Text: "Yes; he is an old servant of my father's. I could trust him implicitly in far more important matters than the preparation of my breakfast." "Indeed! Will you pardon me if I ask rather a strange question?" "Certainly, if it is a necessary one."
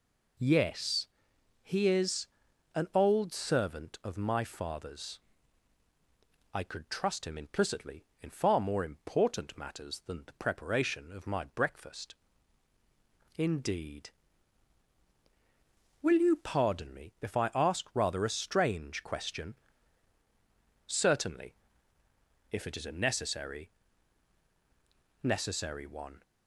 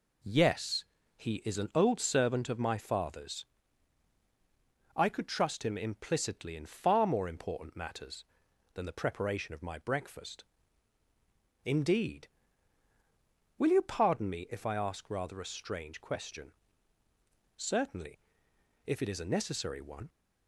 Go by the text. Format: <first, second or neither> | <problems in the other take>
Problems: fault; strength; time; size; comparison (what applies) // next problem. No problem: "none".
second | pauses between "is" and "an"; noticeable; at 2.2 s; 0.46 s long // says "necessary" twice; at 25.2 s